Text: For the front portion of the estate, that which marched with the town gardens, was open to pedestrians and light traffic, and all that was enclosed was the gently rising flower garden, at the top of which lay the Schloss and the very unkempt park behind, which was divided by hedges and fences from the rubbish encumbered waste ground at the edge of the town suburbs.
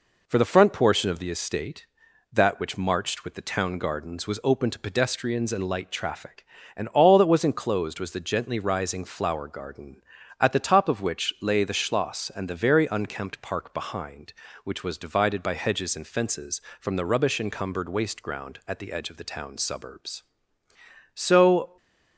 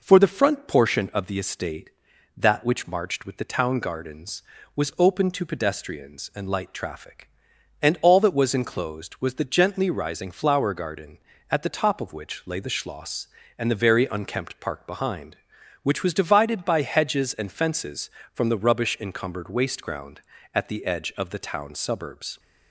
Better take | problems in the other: second | goes on to say "So"; noticeable; from 21.1 s on; 0.62 s long // stays silent after the last word; slight; from 21.6 s on; 0.5 s long

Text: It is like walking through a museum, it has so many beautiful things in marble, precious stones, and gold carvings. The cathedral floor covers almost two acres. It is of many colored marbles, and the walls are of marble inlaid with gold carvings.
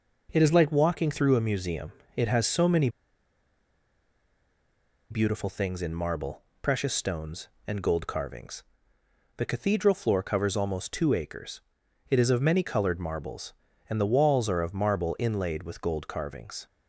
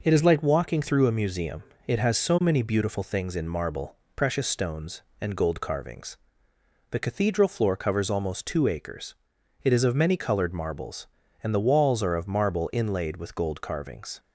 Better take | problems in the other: second | pauses between "many" and "beautiful"; strong; at 2.8 s; 2.2 s long

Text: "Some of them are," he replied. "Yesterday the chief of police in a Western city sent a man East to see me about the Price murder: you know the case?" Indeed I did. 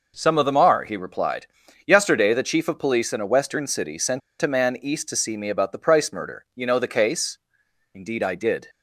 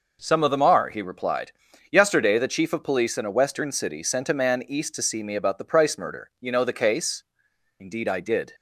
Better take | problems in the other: second | pauses between "sent" and "a"; slight; at 4.2 s; 0.21 s long

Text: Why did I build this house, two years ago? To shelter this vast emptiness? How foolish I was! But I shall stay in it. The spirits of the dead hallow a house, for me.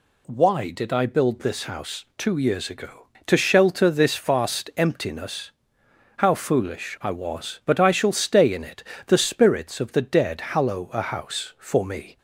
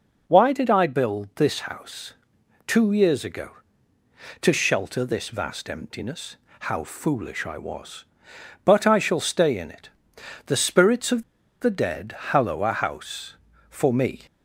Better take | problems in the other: first | pauses between "of" and "the"; at 11.2 s; 0.38 s long

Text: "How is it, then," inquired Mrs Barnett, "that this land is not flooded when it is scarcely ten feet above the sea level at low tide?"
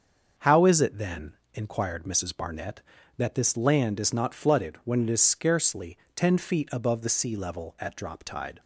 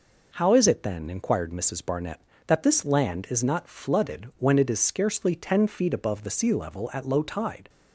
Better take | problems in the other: second | starts louder than the rest; until 1.5 s; 6.5 dB // pauses between "scarcely" and "ten"; slight; at 5.9 s; 0.20 s long // says "drop" for "low"; at 7.9 s

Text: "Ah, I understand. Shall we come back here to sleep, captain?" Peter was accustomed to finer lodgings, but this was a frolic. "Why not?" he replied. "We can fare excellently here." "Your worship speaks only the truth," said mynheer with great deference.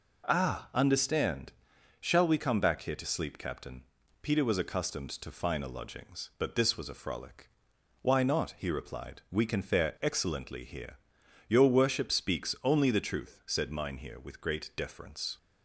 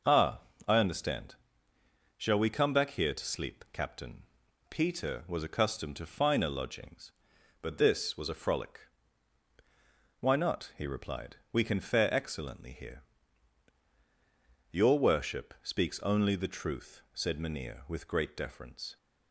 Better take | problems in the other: second | skips "I"; at 0.7 s

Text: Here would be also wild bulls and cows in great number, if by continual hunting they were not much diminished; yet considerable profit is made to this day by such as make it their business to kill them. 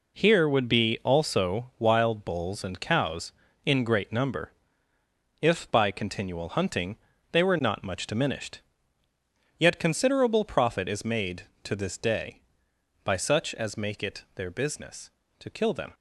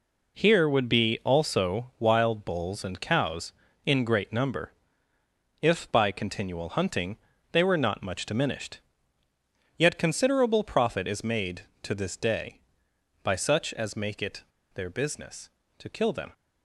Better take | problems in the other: first | pauses between "hunting" and "they"; slight; at 7.1 s; 0.36 s long; slight in the first // pauses between "it" and "their"; slight; at 14.4 s; 0.32 s long

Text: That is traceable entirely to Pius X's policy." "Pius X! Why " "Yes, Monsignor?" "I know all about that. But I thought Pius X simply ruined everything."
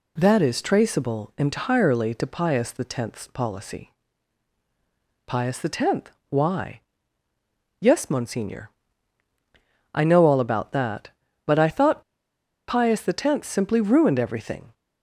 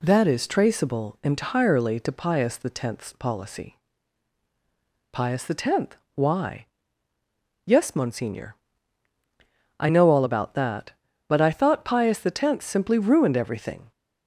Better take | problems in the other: second | pauses between "thought" and "Pius"; noticeable; at 12.0 s; 0.67 s long

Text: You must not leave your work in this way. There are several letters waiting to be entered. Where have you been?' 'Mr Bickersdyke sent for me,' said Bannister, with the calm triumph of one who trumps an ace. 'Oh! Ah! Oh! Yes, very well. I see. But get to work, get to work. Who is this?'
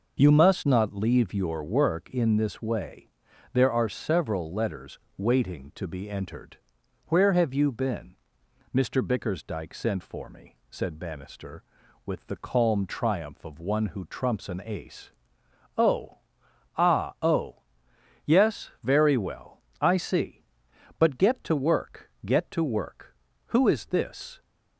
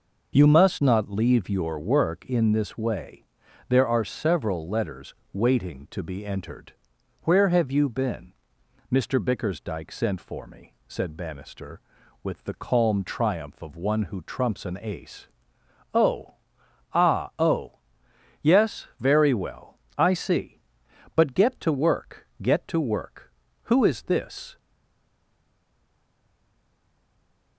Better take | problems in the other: first | pauses between "letters" and "waiting"; slight; at 5.1 s; 0.18 s long; slight in the first // stays silent after the last word; strong; from 24.5 s on; 3.0 s long

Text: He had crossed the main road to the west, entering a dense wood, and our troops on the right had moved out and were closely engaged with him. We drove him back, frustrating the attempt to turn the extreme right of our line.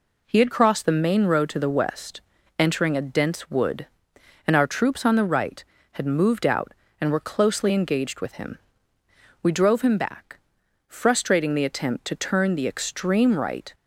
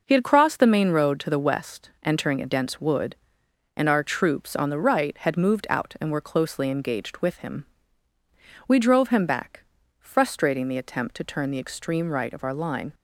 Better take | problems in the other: second | stops before "of our line"; at 13.7 s

